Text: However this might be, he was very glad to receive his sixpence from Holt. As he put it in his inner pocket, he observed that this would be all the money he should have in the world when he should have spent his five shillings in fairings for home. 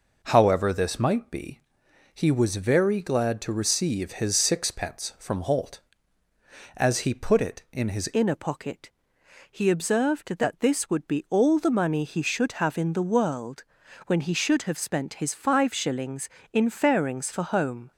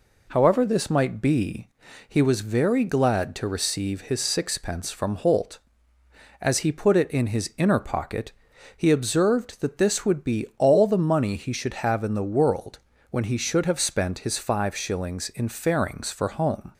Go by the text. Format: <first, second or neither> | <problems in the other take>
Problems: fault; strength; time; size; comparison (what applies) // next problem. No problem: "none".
second | changes voice at "inner"; from 8.1 s on; 9.8 s long // pauses between "world" and "when"; at 13.6 s; 0.44 s long; slight in the second